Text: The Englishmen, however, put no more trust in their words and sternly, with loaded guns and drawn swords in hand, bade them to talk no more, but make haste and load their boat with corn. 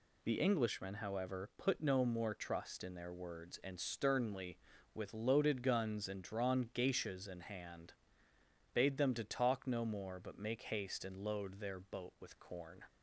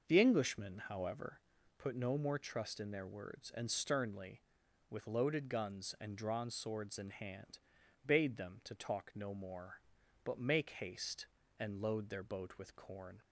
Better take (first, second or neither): second